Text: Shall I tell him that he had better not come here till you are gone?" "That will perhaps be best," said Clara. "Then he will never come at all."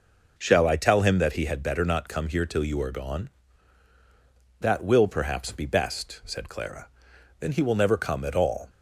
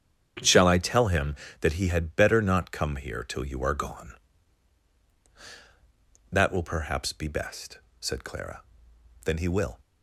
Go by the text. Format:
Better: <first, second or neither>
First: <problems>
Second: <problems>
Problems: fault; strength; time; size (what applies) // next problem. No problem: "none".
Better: first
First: none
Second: starts louder than the rest; strong; until 1.6 s; 8.5 dB // stops before "never come at all"; at 9.7 s